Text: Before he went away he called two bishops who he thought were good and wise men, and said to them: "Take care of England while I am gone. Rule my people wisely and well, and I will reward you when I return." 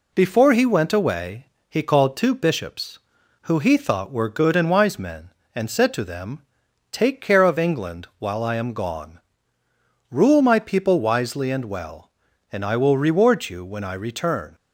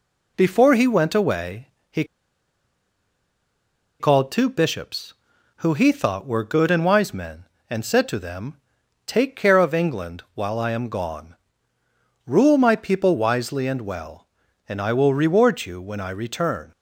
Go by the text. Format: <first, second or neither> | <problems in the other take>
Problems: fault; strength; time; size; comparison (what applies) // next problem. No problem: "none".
first | pauses between "away" and "he"; slight; at 1.6 s; 0.22 s long; slight in the first // pauses between "he" and "called"; strong; at 2.0 s; 1.9 s long